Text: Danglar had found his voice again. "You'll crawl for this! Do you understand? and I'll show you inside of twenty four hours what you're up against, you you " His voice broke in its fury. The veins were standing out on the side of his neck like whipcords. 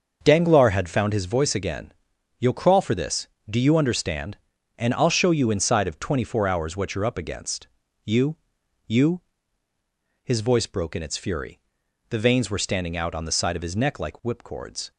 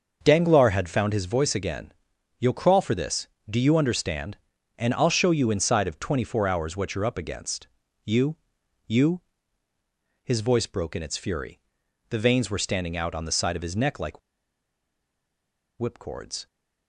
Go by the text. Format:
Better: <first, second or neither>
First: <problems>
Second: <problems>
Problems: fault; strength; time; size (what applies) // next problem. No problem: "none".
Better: first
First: starts louder than the rest; until 1.2 s; 6.5 dB // pauses between "you" and "you"; noticeable; at 8.3 s; 0.50 s long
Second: starts louder than the rest; until 1.2 s; 6.5 dB // pauses between "you" and "you"; noticeable; at 8.3 s; 0.50 s long // pauses between "like" and "whipcords"; strong; at 14.1 s; 1.5 s long